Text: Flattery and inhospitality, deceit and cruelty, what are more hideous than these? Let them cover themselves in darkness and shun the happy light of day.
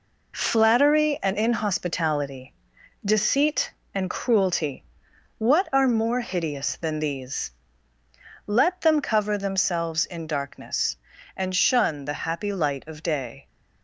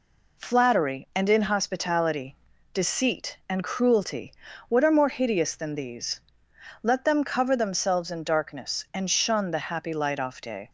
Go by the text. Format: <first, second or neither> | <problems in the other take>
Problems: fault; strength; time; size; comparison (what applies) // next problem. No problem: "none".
first | says "off" for "of"; at 10.1 s